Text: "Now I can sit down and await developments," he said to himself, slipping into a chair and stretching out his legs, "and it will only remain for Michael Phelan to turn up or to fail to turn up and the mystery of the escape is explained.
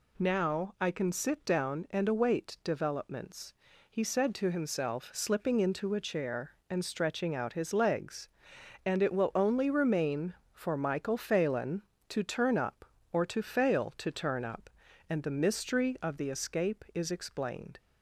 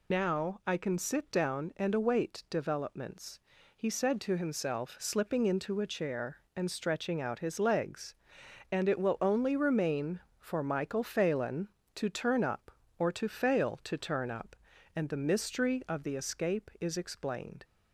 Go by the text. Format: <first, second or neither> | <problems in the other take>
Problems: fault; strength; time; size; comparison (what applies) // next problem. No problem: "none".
first | loses the start of "Now"; at 0.1 s; 80 ms